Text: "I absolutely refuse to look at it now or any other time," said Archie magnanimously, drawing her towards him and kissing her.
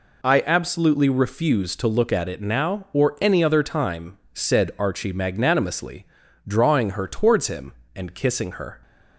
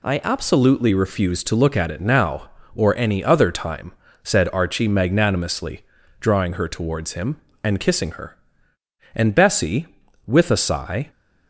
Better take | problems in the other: first | goes on to say "And Bessie with a sigh"; strong; from 9.1 s on; 1.9 s long

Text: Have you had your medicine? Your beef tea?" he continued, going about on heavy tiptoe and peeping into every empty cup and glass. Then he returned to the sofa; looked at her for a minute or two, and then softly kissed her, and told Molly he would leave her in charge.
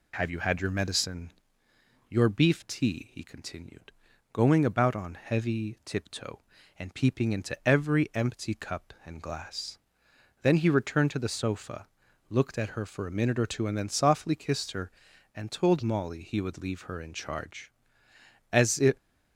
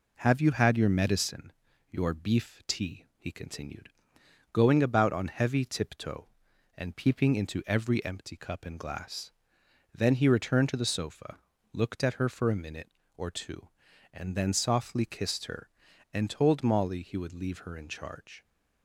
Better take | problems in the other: second | goes on to say "As if"; slight; from 18.5 s on; 0.42 s long

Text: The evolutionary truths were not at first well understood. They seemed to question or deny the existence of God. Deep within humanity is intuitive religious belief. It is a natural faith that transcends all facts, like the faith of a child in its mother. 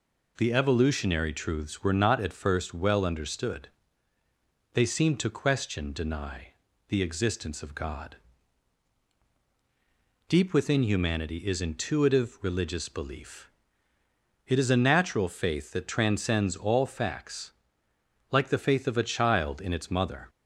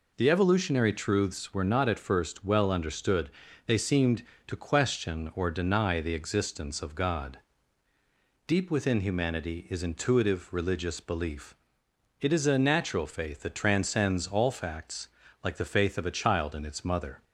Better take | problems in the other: second | skips "or"; at 5.9 s // pauses between "deny" and "the"; at 6.4 s; 0.42 s long

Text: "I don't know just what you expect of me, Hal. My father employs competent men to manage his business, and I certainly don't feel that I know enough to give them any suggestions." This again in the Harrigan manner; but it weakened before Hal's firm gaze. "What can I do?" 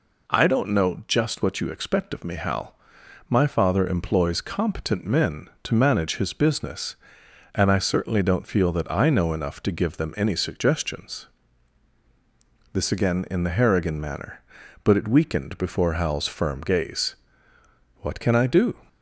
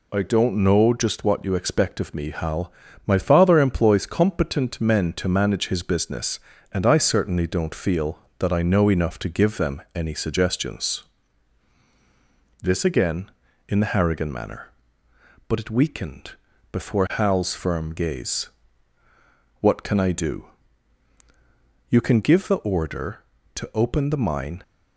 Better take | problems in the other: first | pauses between "weakened" and "before"; at 16.3 s; 0.40 s long // goes on to say "You can give the order to open the mine"; strong; from 21.8 s on; 2.7 s long

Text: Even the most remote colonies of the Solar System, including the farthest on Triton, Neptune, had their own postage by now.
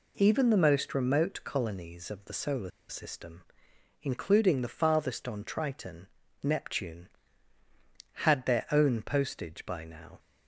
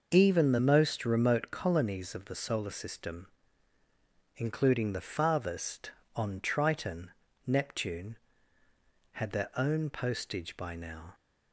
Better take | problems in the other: second | pauses between "Solar" and "System"; slight; at 2.6 s; 0.19 s long

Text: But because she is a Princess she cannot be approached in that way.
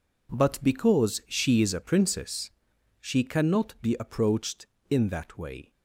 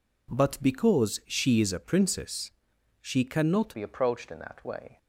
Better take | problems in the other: first | pauses between "Princess" and "she"; noticeable; at 2.5 s; 0.50 s long; noticeable in the first // changes voice at "be"; from 3.7 s on; 1.2 s long

